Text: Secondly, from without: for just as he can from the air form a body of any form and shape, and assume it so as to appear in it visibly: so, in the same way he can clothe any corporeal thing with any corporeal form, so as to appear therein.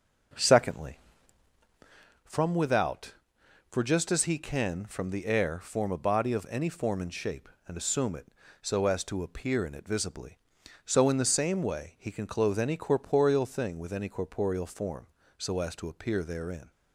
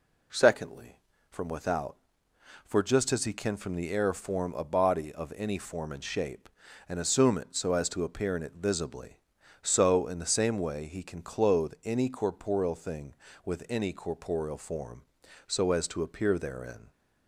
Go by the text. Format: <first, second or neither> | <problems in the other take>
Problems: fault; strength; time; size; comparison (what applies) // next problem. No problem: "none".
second | starts louder than the rest; noticeable; until 2.1 s; 6 dB